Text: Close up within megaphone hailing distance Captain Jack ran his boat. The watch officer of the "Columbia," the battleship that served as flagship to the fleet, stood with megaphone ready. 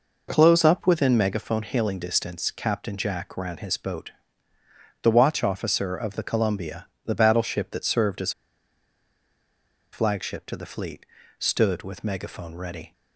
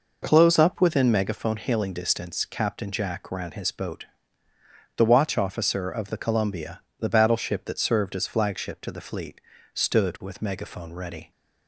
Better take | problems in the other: second | pauses between "as" and "flagship"; strong; at 8.3 s; 1.6 s long

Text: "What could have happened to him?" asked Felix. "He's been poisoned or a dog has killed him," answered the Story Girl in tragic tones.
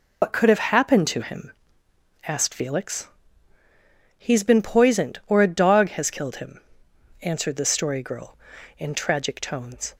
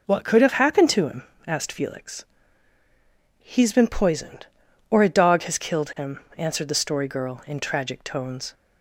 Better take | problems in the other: second | loses the start of "What"; at 0.2 s; 75 ms

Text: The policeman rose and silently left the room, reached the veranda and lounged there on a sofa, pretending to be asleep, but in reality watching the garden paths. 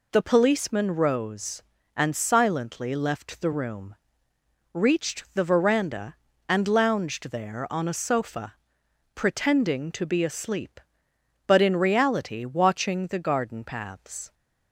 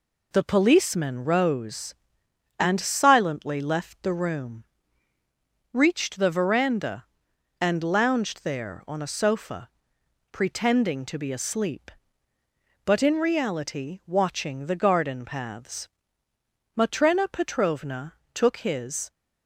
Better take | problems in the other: first | goes on to say "Matrena Petrovna took his"; strong; from 16.7 s on; 2.3 s long

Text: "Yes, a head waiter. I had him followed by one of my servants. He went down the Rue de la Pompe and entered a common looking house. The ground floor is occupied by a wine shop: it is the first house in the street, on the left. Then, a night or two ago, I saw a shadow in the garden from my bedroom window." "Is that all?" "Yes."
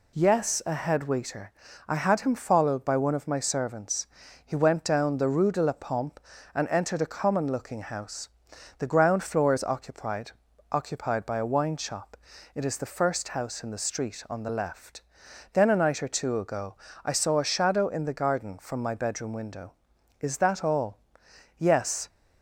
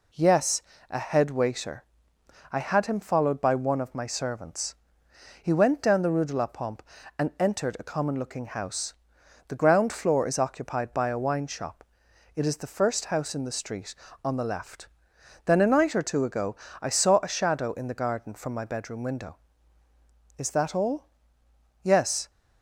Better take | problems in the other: second | says "occupied" twice; at 10.6 s

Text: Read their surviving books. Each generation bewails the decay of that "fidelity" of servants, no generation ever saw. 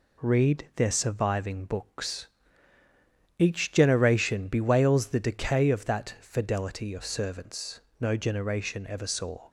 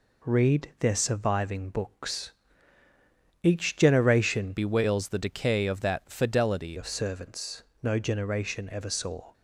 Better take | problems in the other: first | changes voice from "bewails" to "fidelity"; from 4.5 to 6.7 s; 2.2 s long

